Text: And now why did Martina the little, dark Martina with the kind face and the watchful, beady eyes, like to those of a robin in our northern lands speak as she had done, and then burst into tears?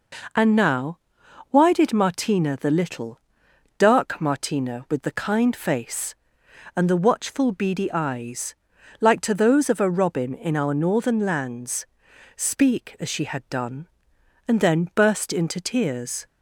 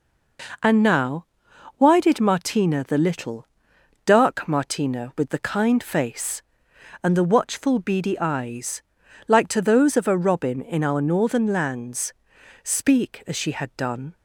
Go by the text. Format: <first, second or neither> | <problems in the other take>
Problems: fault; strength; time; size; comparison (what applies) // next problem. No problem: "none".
first | pauses between "now" and "why"; noticeable; at 1.2 s; 0.54 s long; noticeable in the first // pauses between "lands" and "speak"; noticeable; at 12.1 s; 0.50 s long; noticeable in the first // stops before "and then burst into tears"; at 14.1 s